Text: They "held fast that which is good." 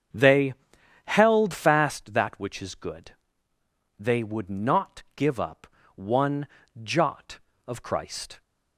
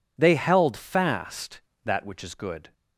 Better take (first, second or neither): second